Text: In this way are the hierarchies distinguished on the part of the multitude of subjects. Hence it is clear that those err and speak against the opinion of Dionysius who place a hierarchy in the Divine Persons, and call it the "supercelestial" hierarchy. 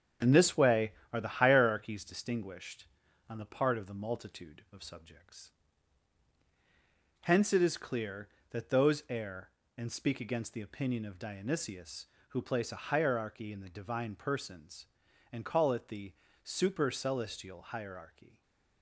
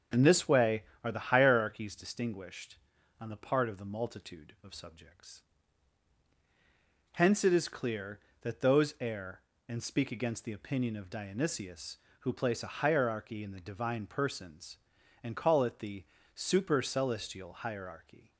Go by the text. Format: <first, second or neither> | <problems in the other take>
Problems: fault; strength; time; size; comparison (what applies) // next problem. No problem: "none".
second | gets quieter; noticeable; throughout; 5.5 dB // starts louder than the rest; strong; until 1.4 s; 7.5 dB; also in the second // pauses between "the" and "supercelestial"; slight; at 16.1 s; 0.32 s long; slight in the second // stays silent after the last word; slight; from 18.2 s on; 0.6 s long